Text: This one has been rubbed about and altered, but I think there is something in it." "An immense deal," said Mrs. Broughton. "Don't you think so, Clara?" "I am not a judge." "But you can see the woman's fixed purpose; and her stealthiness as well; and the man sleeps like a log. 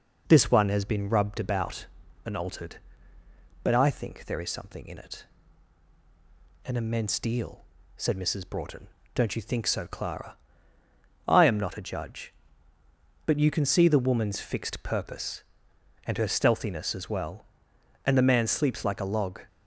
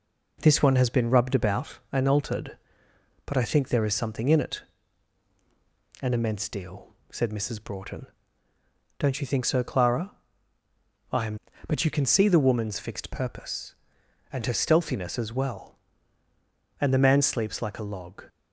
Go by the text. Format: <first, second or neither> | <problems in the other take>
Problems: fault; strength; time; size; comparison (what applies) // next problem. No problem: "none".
first | skips "not a judge"; at 11.5 s